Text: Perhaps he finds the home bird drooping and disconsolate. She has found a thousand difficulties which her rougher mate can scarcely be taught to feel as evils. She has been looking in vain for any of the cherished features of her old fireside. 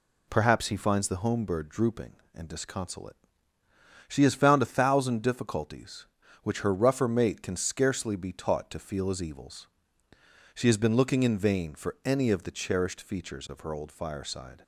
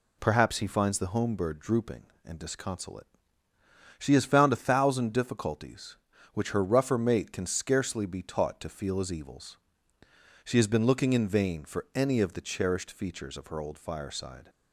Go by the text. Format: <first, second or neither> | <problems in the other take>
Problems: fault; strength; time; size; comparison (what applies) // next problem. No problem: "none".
neither | none